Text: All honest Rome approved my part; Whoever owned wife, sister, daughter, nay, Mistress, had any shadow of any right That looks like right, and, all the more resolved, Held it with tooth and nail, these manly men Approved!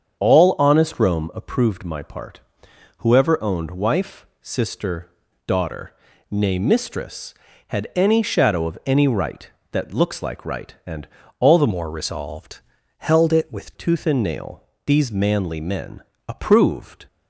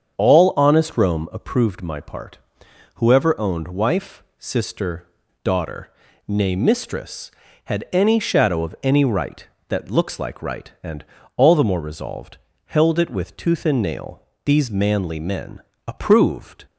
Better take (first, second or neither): second